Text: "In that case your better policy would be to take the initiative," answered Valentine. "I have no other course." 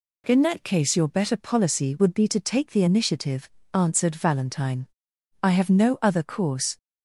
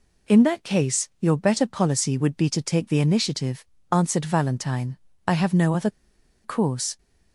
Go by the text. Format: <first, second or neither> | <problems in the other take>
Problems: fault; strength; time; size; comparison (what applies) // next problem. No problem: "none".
first | pauses between "other" and "course"; noticeable; at 5.9 s; 0.54 s long